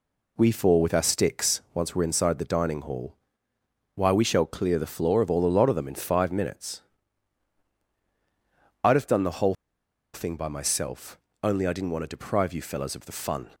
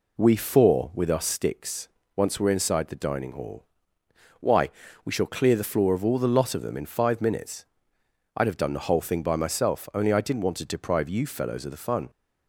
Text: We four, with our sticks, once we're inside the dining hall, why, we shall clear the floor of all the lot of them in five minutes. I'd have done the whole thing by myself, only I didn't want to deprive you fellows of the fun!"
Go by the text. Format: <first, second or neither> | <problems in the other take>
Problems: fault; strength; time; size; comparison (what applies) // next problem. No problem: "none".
second | pauses between "whole" and "thing"; noticeable; at 9.5 s; 0.59 s long